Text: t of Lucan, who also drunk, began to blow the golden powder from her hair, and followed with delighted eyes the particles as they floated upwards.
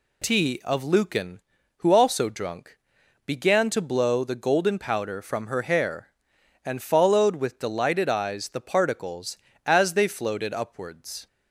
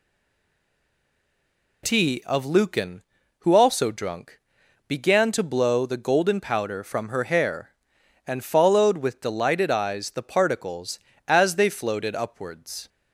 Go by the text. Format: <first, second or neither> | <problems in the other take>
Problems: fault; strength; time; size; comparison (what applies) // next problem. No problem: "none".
first | stays silent before the first word; noticeable; until 1.8 s; 1.8 s long